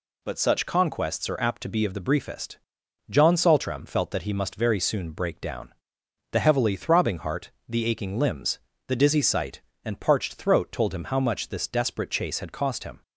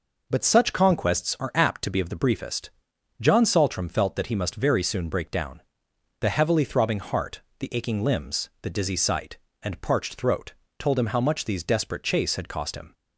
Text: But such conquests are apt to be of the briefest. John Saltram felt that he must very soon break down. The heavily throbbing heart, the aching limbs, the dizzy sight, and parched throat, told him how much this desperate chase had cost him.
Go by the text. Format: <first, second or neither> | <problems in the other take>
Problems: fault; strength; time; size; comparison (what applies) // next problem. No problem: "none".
first | says "these" for "this"; at 11.4 s